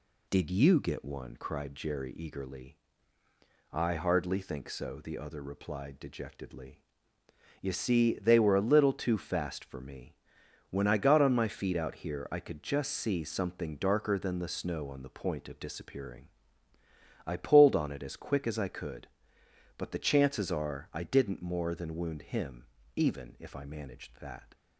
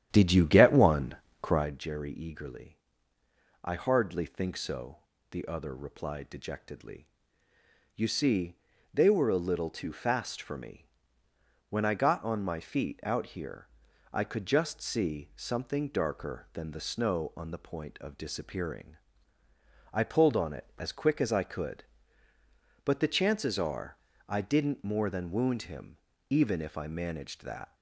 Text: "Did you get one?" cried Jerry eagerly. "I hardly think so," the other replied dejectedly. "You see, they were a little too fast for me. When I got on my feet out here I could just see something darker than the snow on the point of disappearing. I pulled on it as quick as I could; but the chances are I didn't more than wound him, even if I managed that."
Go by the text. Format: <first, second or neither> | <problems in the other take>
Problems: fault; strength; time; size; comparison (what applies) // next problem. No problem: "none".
first | starts louder than the rest; strong; until 1.7 s; 10.5 dB // pauses between "here" and "I"; at 13.6 s; 0.44 s long // pauses between "are" and "I"; slight; at 23.9 s; 0.32 s long